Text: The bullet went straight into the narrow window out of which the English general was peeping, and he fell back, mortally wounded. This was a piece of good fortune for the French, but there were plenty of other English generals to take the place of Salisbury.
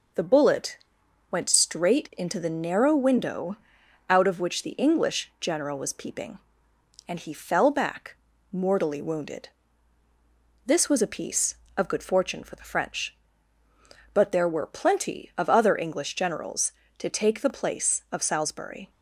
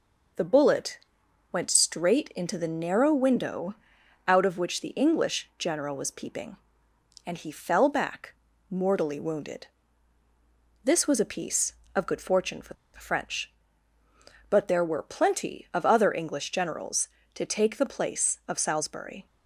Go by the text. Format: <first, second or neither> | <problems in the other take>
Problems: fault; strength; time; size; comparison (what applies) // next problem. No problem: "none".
first | pauses between "bullet" and "went"; noticeable; at 0.9 s; 0.54 s long; noticeable in the first // pauses between "window" and "out"; noticeable; at 3.7 s; 0.52 s long; noticeable in the first // pauses between "for" and "the"; slight; at 12.7 s; 0.20 s long